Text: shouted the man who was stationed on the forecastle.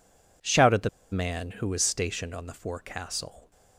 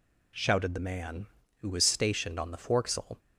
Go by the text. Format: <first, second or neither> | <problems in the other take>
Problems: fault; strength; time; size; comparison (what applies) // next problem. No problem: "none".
second | pauses between "the" and "man"; slight; at 0.8 s; 0.23 s long